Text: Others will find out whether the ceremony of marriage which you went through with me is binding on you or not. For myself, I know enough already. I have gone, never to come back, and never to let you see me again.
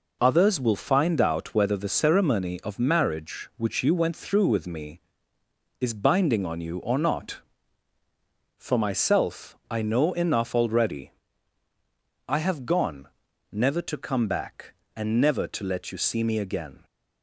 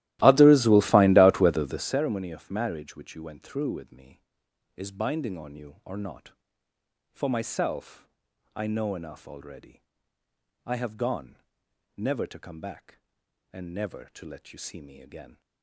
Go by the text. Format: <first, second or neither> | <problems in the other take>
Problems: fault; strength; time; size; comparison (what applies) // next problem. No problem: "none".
first | starts louder than the rest; strong; until 2.0 s; 16 dB